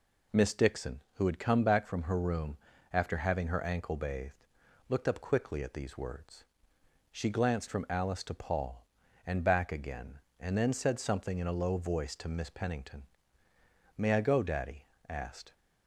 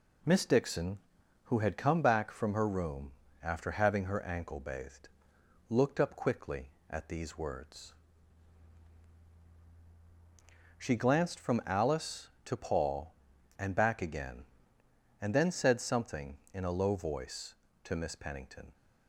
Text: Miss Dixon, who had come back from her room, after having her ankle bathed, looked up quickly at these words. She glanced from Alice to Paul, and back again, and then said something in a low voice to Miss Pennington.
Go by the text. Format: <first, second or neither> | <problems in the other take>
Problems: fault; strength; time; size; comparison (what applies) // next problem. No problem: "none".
second | goes on to say "May I go Daddy asked"; from 13.9 s on; 1.5 s long